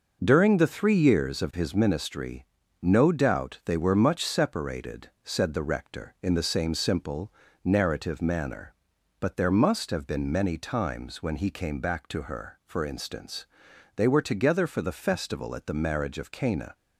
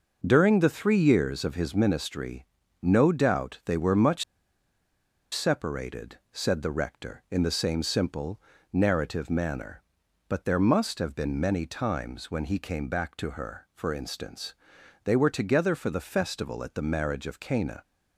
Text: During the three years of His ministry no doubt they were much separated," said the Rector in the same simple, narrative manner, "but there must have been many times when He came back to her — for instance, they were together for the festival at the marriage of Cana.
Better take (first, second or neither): first